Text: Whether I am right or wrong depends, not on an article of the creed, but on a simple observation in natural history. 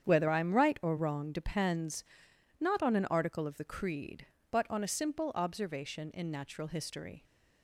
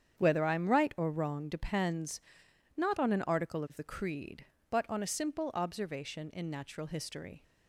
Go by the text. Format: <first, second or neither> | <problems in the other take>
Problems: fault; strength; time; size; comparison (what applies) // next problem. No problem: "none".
neither | starts louder than the rest; strong; the same in both